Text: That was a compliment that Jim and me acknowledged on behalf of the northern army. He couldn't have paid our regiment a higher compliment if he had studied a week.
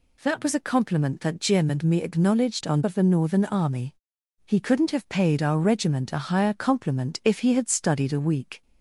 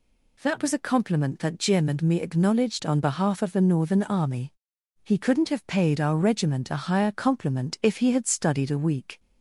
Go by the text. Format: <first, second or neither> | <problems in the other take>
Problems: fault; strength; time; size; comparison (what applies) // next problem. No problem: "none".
second | skips "behalf"; at 2.8 s